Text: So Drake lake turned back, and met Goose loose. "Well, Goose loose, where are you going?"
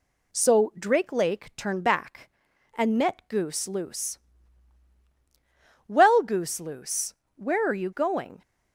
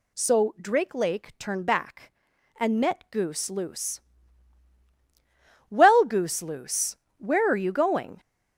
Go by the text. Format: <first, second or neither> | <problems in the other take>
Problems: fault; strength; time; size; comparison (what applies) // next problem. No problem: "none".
first | gets louder; noticeable; throughout; 6 dB